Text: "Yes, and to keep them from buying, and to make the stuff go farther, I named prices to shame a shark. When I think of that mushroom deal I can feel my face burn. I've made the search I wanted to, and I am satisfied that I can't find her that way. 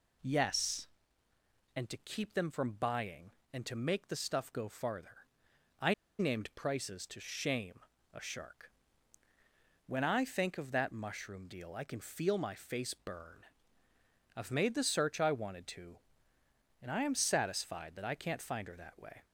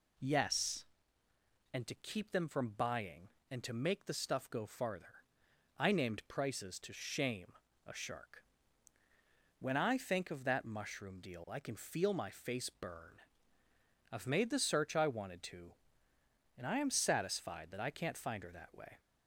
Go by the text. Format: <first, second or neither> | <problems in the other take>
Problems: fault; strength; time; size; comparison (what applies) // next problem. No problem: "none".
second | pauses between "I" and "named"; slight; at 5.9 s; 0.25 s long // pauses between "shame" and "a"; slight; at 7.7 s; 0.32 s long; slight in the second